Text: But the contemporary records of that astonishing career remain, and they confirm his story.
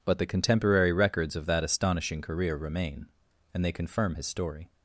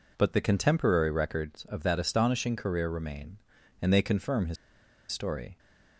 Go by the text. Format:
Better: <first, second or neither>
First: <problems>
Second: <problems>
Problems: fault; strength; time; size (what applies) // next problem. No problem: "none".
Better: first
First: none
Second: pauses between "his" and "story"; noticeable; at 4.5 s; 0.56 s long